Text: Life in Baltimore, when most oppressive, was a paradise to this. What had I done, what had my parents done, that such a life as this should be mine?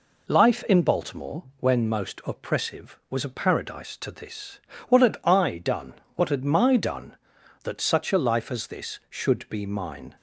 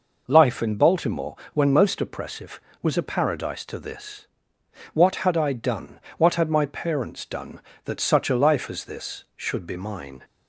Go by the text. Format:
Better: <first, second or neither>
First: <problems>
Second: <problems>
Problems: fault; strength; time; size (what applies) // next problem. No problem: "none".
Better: second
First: skips "parents"; at 6.7 s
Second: none